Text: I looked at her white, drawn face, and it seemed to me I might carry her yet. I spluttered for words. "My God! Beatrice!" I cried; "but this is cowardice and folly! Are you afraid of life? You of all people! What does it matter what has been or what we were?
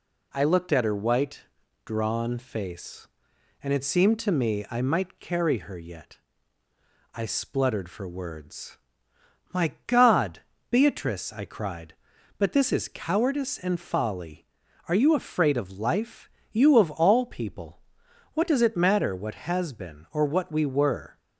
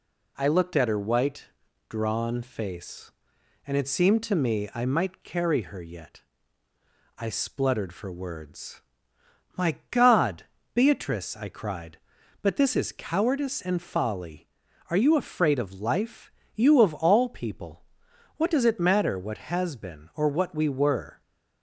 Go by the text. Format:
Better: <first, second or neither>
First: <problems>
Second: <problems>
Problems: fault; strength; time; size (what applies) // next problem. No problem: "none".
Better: neither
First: pauses between "My" and "God"; slight; at 9.7 s; 0.16 s long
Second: pauses between "My" and "God"; slight; at 9.7 s; 0.16 s long